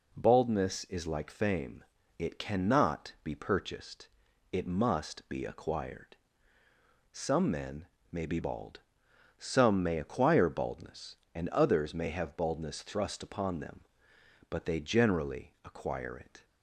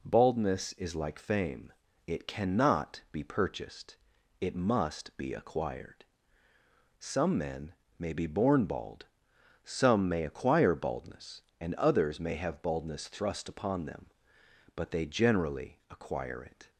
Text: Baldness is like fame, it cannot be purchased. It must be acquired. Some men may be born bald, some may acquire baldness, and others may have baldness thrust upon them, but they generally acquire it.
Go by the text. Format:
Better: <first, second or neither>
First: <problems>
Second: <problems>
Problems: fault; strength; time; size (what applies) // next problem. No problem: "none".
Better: second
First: pauses between "men" and "may"; slight; at 7.8 s; 0.24 s long // skips "born"; at 8.3 s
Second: pauses between "men" and "may"; slight; at 7.7 s; 0.24 s long